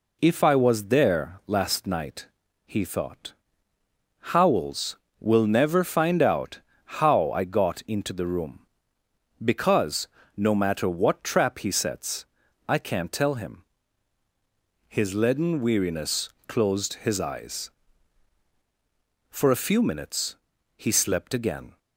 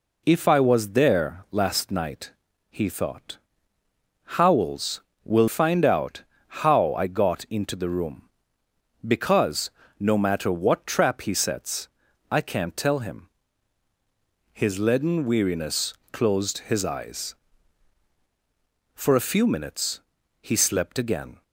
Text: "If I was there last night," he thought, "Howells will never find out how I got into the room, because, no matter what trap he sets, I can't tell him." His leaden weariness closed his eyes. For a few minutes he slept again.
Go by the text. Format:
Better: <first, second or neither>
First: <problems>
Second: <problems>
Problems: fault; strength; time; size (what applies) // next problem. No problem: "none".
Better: first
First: pauses between "out" and "how"; at 6.5 s; 0.40 s long // pauses between "weariness" and "closed"; slight; at 16.3 s; 0.18 s long // pauses between "minutes" and "he"; at 20.3 s; 0.42 s long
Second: skips "never"; at 5.4 s // pauses between "out" and "how"; at 6.2 s; 0.40 s long // pauses between "weariness" and "closed"; slight; at 15.9 s; 0.18 s long // pauses between "minutes" and "he"; at 19.9 s; 0.42 s long